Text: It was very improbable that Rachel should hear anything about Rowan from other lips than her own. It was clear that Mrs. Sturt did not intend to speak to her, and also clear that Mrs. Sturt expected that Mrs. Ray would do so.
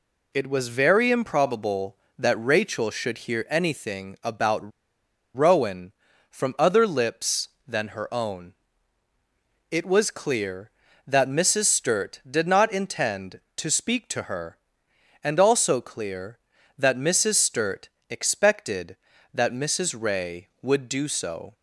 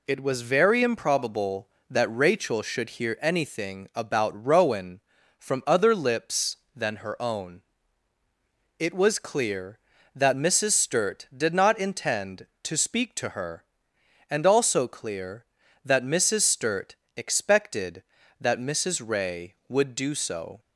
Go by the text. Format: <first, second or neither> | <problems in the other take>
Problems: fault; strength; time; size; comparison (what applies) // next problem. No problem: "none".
second | pauses between "about" and "Rowan"; noticeable; at 4.7 s; 0.66 s long // pauses between "Sturt" and "expected"; slight; at 17.8 s; 0.20 s long; slight in the second